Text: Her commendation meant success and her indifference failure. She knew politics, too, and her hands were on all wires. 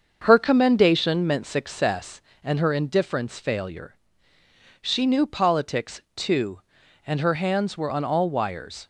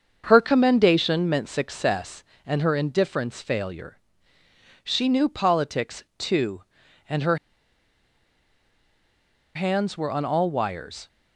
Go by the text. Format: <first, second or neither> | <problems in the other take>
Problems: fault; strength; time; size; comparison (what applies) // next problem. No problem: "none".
first | starts louder than the rest; until 1.2 s; 6.5 dB; also in the first // pauses between "her" and "hands"; strong; at 7.3 s; 2.1 s long